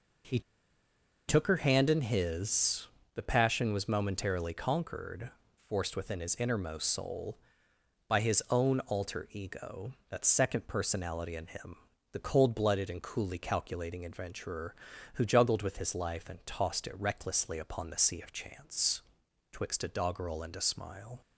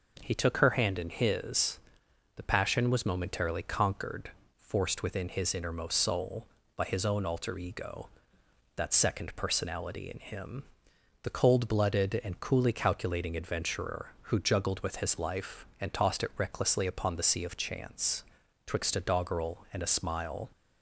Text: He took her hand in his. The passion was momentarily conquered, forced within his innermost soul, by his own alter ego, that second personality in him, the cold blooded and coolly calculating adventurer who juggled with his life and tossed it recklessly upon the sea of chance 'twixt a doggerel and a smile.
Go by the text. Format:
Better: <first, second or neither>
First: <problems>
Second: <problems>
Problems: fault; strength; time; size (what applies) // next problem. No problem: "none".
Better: second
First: pauses between "He" and "took"; noticeable; at 0.3 s; 0.87 s long // pauses between "chance" and "twixt"; noticeable; at 19.0 s; 0.50 s long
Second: pauses between "chance" and "twixt"; at 18.2 s; 0.44 s long